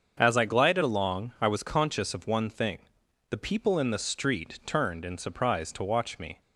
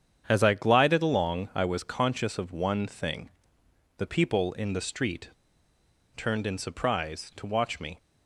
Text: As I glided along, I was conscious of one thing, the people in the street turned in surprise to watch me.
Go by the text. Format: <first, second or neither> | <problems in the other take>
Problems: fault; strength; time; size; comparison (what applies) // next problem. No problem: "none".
first | starts louder than the rest; strong; until 1.2 s; 8 dB; also in the first // pauses between "street" and "turned"; noticeable; at 5.2 s; 0.86 s long